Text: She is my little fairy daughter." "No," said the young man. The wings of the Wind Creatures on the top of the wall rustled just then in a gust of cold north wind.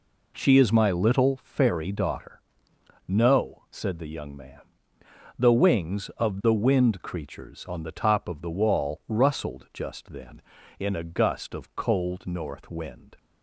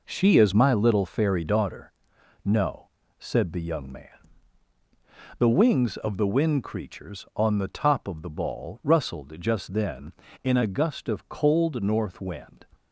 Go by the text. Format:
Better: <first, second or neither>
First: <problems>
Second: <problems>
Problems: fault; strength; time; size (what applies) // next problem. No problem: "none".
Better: first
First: none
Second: says "ball" for "wall"; at 8.2 s